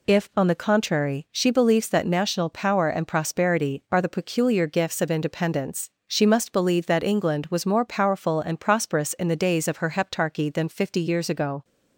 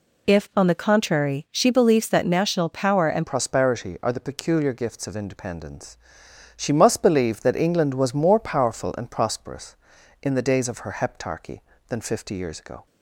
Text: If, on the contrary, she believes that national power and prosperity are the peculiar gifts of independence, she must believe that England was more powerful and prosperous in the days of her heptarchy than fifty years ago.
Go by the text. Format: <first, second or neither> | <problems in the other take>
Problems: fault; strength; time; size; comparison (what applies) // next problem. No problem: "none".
first | changes voice at "prosperity"; from 3.2 s on; 9.6 s long